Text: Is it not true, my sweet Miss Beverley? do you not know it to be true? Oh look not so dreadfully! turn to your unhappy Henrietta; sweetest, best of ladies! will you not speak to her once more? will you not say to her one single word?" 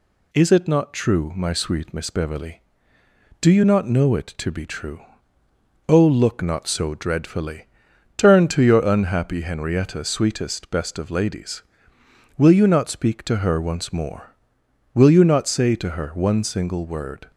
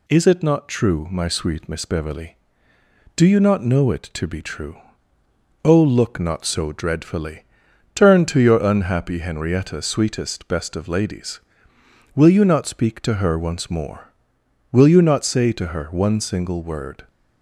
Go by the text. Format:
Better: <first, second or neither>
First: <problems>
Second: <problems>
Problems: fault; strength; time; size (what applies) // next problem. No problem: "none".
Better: neither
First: none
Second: none